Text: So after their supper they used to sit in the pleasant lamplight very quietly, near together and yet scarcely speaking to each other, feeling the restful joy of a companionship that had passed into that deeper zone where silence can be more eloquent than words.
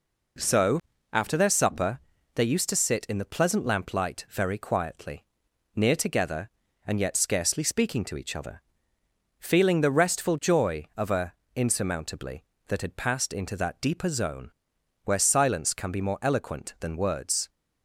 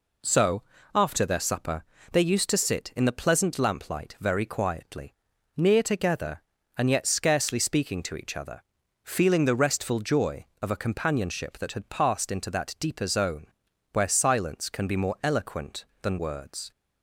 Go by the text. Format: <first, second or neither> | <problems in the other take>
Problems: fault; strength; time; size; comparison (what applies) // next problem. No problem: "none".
second | pauses between "So" and "after"; slight; at 0.7 s; 0.32 s long; slight in the second // pauses between "supper" and "they"; slight; at 1.9 s; 0.36 s long; slight in the second // says "insurmountably" for "companionship"; at 11.5 s // pauses between "zone" and "where"; noticeable; at 14.5 s; 0.52 s long; noticeable in the second